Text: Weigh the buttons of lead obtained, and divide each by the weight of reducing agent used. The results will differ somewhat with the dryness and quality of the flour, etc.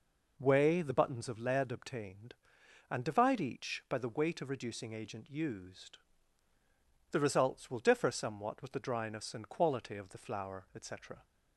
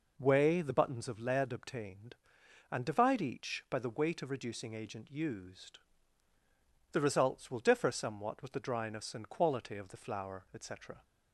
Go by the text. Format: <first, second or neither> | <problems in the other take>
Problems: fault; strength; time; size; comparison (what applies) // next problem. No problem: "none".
neither | none